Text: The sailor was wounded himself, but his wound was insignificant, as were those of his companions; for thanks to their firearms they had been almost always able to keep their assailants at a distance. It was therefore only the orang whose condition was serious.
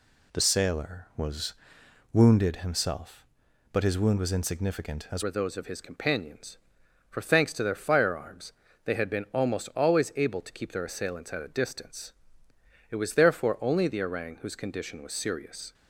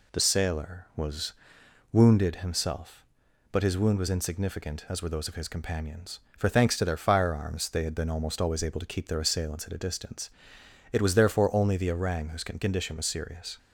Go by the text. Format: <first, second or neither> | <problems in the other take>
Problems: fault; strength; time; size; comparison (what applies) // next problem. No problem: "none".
second | pauses between "was" and "wounded"; noticeable; at 1.5 s; 0.58 s long; noticeable in the second // changes voice at "were"; from 5.2 s on; 10.5 s long // pauses between "firearms" and "they"; slight; at 8.5 s; 0.32 s long